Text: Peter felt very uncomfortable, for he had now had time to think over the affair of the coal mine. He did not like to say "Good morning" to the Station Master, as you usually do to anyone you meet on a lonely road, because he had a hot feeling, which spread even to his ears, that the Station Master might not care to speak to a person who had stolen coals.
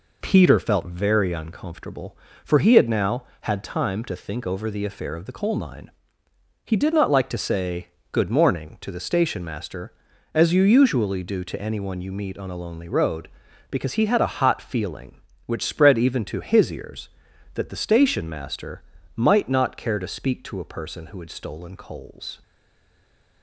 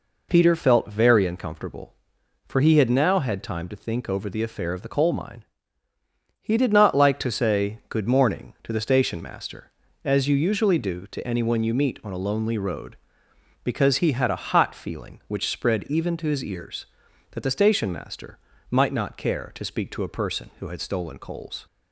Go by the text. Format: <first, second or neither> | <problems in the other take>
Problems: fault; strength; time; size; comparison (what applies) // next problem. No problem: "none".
second | pauses between "say" and "Good"; slight; at 7.8 s; 0.24 s long // pauses between "Master" and "might"; slight; at 18.8 s; 0.32 s long; slight in the second // stays silent after the last word; from 22.4 s on; 1.0 s long